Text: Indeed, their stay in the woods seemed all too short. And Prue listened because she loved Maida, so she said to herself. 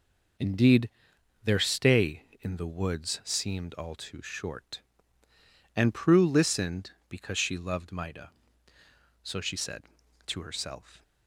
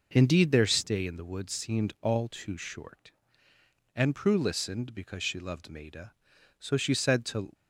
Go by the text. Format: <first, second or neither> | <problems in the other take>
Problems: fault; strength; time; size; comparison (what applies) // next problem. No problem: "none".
first | stops before "herself"; at 7.5 s